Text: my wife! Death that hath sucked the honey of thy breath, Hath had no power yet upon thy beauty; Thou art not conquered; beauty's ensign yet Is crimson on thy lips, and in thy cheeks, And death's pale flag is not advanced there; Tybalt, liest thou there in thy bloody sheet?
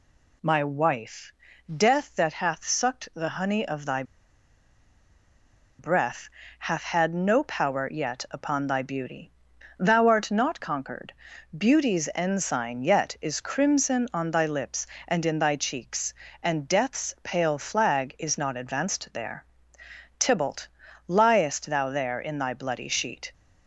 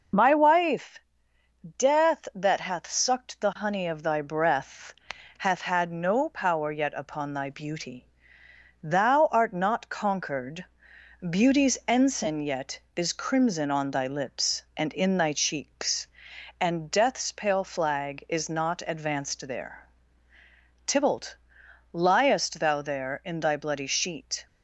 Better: second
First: pauses between "thy" and "breath"; strong; at 4.0 s; 1.7 s long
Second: none

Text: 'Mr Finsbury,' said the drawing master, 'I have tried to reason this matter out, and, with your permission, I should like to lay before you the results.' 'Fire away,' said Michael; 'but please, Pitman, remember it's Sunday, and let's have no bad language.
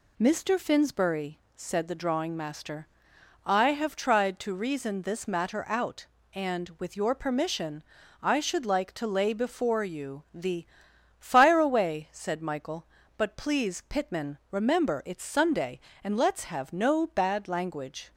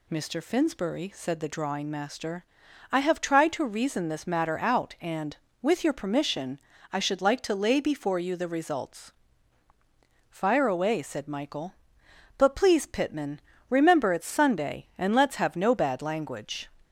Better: second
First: skips "results"; at 10.9 s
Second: none

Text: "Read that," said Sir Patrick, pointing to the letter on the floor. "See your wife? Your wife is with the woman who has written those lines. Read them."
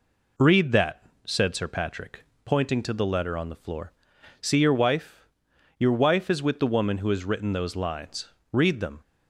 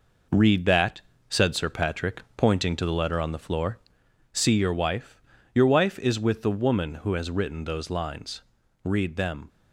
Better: first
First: none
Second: gets quieter; strong; throughout; 7.5 dB

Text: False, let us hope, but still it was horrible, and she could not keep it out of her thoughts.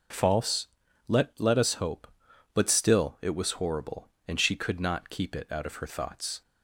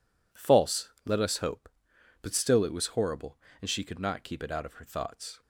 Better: second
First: says "let" twice; at 1.3 s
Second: none

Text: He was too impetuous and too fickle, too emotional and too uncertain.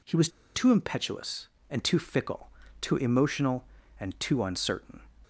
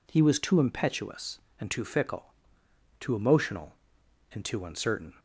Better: second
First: pauses between "was" and "too"; slight; at 0.2 s; 0.25 s long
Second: none

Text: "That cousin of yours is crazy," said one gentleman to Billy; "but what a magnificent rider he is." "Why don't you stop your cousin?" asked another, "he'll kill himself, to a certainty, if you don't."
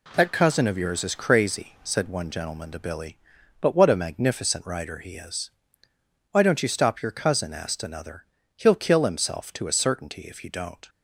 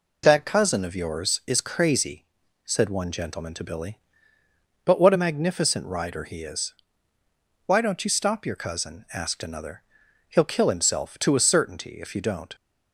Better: neither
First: none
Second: none

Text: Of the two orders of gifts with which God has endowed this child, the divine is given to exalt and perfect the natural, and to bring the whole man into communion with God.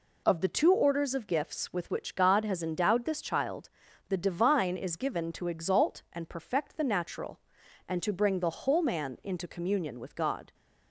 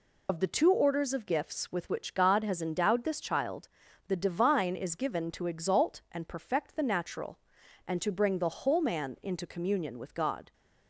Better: first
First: none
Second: loses the start of "Of"; at 0.2 s; 50 ms

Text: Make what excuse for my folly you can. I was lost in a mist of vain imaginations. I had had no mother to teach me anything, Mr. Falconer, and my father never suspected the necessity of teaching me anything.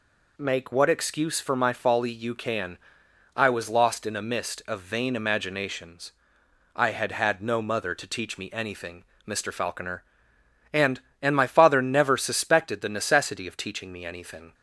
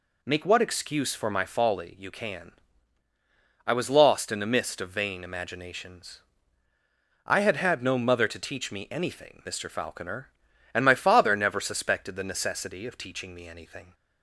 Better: second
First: says "and" twice; at 11.2 s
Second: none

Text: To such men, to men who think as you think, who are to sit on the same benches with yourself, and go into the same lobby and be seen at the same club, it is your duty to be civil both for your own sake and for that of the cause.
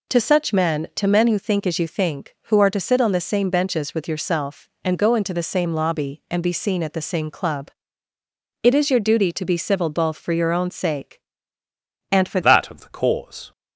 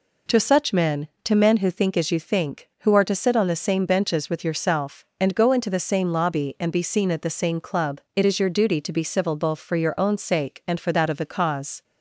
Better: second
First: changes voice at "that"; from 12.4 s on; 1.1 s long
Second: none

